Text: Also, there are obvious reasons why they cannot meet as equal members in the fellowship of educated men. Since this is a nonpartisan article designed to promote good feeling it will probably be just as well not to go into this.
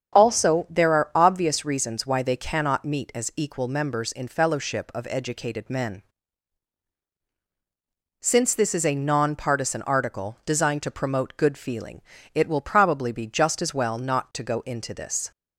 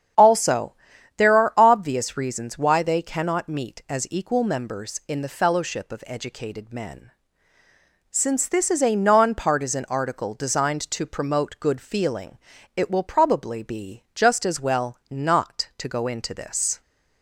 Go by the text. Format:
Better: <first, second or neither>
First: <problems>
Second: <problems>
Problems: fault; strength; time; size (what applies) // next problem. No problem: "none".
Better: second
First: starts louder than the rest; strong; until 1.2 s; 7.5 dB // skips "the"; at 4.2 s // pauses between "feeling" and "it"; slight; at 11.9 s; 0.34 s long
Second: starts louder than the rest; strong; until 1.6 s; 8.5 dB // pauses between "feeling" and "it"; slight; at 12.3 s; 0.36 s long